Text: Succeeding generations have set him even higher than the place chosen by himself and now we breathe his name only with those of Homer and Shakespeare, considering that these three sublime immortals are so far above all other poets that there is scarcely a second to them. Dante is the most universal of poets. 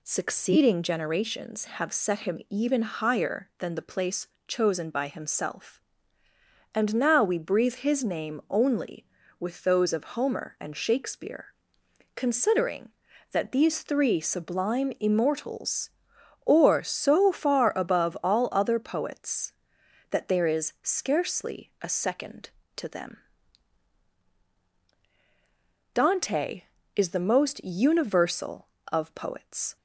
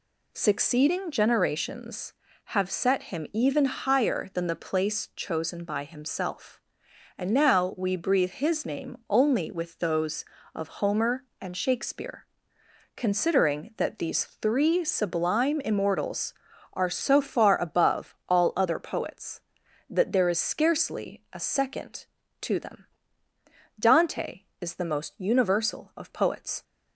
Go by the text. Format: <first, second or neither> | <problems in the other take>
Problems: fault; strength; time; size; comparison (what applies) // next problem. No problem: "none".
second | pauses between "place" and "chosen"; slight; at 4.2 s; 0.22 s long // says "or" for "are"; at 16.4 s